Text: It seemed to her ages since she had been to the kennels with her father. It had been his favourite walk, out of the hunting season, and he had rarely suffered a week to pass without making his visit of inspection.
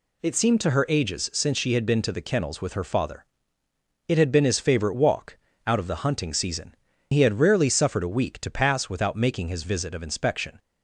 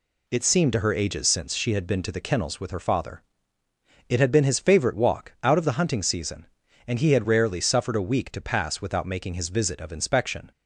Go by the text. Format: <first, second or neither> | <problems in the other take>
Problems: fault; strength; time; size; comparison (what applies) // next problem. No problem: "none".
second | skips "and"; at 6.9 s